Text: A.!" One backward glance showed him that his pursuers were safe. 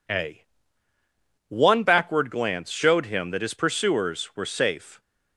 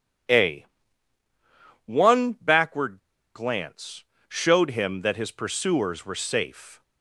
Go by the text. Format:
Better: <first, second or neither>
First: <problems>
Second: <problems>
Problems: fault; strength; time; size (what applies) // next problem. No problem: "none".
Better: first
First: none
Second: pauses between "backward" and "glance"; at 2.9 s; 0.38 s long // pauses between "glance" and "showed"; slight; at 4.0 s; 0.24 s long